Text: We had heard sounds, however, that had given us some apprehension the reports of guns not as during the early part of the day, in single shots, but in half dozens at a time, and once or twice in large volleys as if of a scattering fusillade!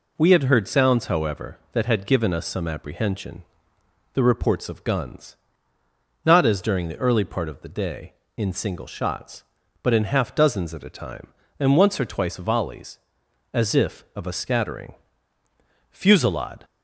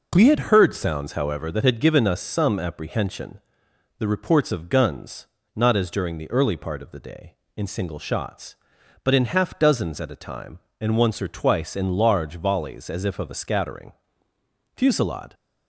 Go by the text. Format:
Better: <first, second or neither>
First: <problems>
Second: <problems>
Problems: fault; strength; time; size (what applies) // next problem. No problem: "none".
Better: second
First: pauses between "apprehension" and "the"; noticeable; at 3.4 s; 0.70 s long // pauses between "guns" and "not"; noticeable; at 5.3 s; 0.88 s long // skips "in large"; at 12.3 s // pauses between "scattering" and "fusillade"; noticeable; at 14.9 s; 0.96 s long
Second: pauses between "apprehension" and "the"; noticeable; at 3.3 s; 0.58 s long // pauses between "guns" and "not"; slight; at 5.2 s; 0.30 s long // pauses between "scattering" and "fusillade"; noticeable; at 13.9 s; 0.84 s long